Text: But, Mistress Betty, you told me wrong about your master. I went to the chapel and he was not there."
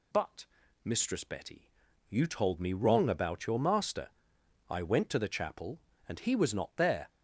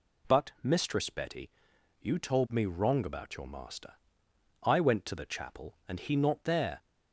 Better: first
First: none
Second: skips "was"; at 6.1 s

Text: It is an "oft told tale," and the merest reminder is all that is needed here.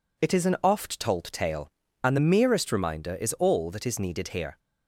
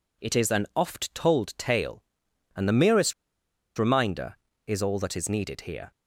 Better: first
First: none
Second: pauses between "merest" and "reminder"; noticeable; at 3.1 s; 0.65 s long

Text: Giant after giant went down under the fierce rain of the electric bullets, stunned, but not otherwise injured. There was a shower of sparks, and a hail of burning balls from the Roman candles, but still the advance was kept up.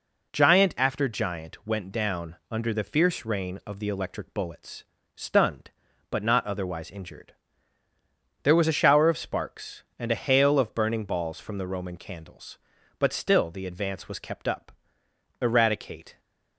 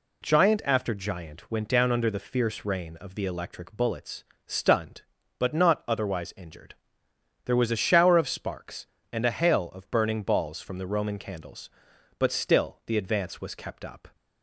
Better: second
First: pauses between "down" and "under"; slight; at 2.3 s; 0.16 s long // goes on to say "Eradicate"; noticeable; from 15.4 s on; 0.78 s long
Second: none

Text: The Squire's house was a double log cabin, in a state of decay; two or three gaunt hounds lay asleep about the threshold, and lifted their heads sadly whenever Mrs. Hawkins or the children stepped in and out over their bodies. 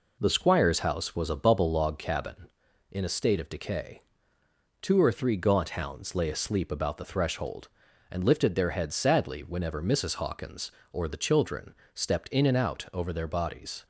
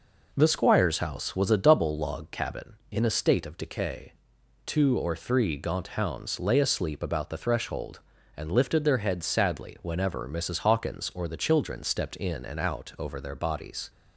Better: second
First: says "bubble" for "double"; at 1.3 s // pauses between "children" and "stepped"; slight; at 11.7 s; 0.22 s long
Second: none

